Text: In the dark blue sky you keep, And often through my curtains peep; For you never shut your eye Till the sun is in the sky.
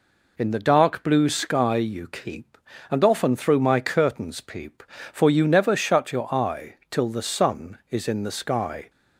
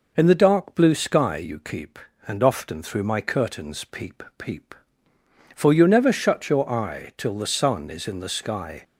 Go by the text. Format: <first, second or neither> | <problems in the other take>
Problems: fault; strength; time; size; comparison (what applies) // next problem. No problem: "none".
first | says "peep" twice; at 4.3 s